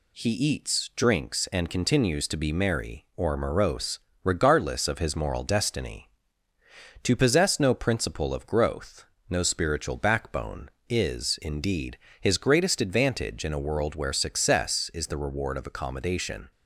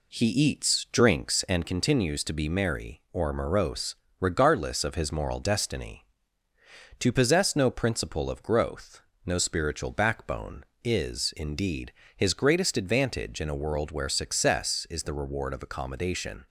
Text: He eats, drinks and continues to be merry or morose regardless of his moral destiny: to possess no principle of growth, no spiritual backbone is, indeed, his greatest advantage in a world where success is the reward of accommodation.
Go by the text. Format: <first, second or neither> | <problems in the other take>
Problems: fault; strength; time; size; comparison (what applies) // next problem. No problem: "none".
first | starts louder than the rest; slight; until 1.7 s; 2.5 dB // pauses between "morose" and "regardless"; slight; at 3.9 s; 0.24 s long; slight in the first